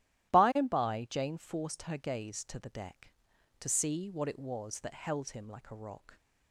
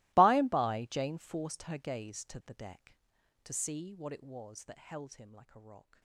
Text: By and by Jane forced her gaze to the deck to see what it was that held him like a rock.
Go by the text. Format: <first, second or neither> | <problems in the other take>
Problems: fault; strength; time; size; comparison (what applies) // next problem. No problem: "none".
first | gets quieter; strong; throughout; 24 dB // starts louder than the rest; strong; until 1.1 s; 22 dB; strong in the first